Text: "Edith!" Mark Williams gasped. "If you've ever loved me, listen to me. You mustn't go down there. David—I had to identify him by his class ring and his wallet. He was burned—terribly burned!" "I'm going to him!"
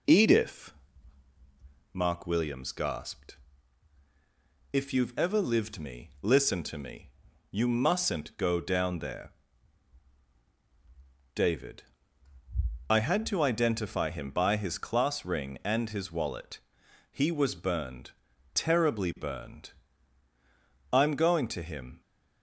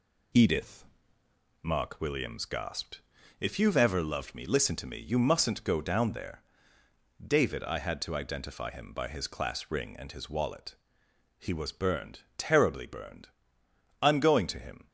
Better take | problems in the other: second | says "lived" for "loved"; at 5.4 s

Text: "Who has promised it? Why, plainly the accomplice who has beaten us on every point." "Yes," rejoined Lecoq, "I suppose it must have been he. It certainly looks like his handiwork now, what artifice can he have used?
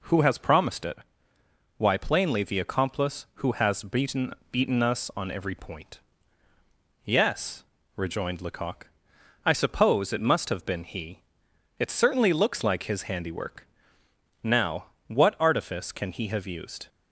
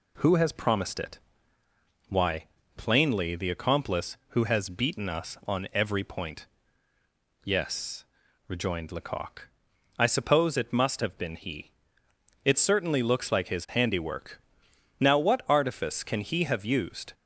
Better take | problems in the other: second | says "beaten" twice; at 4.5 s // pauses between "handiwork" and "now"; noticeable; at 13.6 s; 0.74 s long; noticeable in the second

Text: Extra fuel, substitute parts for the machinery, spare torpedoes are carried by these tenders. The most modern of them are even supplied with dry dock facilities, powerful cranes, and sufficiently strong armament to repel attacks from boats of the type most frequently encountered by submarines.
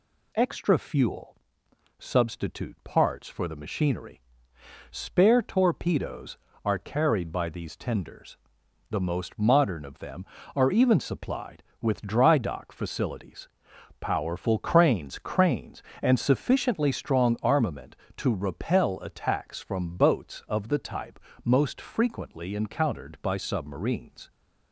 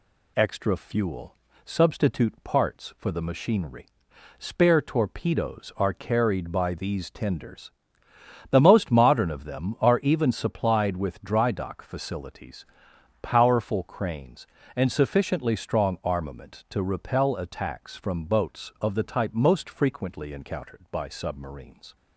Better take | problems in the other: second | says "cranes" twice; at 15.1 s // pauses between "type" and "most"; slight; at 21.1 s; 0.26 s long

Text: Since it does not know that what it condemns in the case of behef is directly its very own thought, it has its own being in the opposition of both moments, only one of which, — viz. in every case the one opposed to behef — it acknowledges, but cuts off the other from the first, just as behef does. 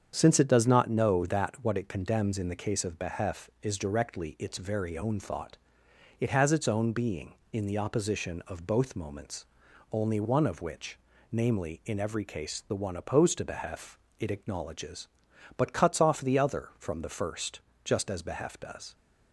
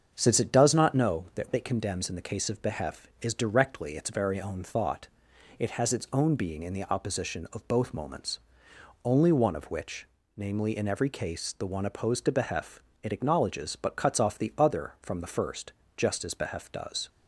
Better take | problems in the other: first | starts louder than the rest; until 1.1 s; 7 dB; strong in the first // skips "what"; at 1.5 s

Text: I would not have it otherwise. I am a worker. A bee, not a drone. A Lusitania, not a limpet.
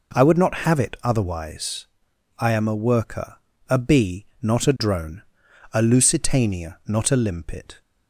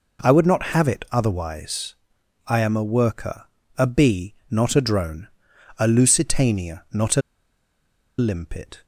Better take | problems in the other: first | pauses between "a" and "limpet"; at 7.2 s; 0.98 s long

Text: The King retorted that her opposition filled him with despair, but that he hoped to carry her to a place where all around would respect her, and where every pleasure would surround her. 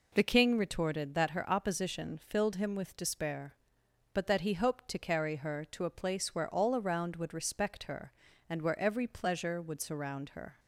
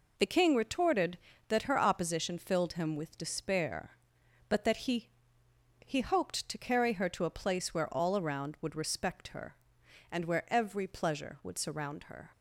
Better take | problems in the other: first | says "he" twice; at 5.8 s

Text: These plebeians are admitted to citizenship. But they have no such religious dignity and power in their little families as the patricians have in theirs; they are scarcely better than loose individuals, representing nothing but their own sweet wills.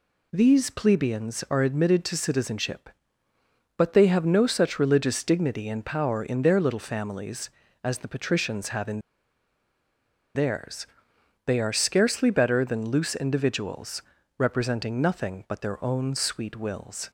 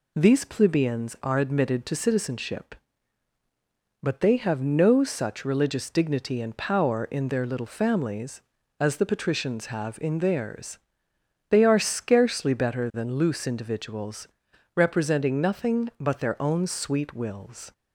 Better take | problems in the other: second | pauses between "in" and "theirs"; strong; at 8.9 s; 1.3 s long

